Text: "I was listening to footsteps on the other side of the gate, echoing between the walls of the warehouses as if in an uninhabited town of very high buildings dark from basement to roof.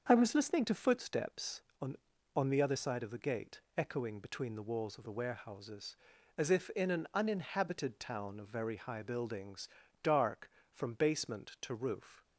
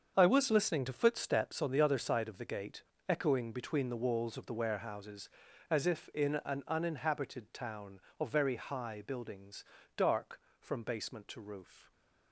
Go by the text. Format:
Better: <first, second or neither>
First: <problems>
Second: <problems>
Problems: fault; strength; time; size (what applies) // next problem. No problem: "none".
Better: second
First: starts louder than the rest; strong; until 1.1 s; 7 dB // says "on" twice; at 2.3 s // pauses between "buildings" and "dark"; slight; at 9.6 s; 0.36 s long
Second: starts louder than the rest; until 1.1 s; 7 dB // pauses between "buildings" and "dark"; slight; at 9.6 s; 0.32 s long